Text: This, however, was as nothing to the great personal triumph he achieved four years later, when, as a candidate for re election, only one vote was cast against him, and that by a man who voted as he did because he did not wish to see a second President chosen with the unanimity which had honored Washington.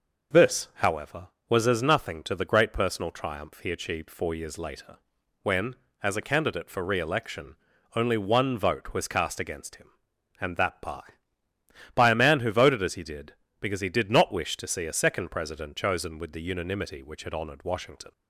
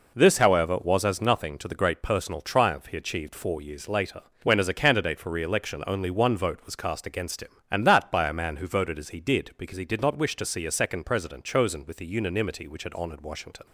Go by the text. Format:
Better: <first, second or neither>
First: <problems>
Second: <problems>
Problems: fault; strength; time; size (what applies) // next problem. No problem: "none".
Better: second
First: says "by" twice; at 11.9 s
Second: none